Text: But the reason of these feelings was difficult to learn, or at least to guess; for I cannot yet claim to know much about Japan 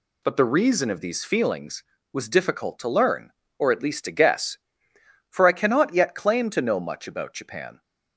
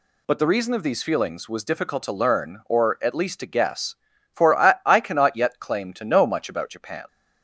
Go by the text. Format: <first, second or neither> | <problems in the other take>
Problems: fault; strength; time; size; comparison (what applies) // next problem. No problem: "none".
first | says "I" twice; at 4.8 s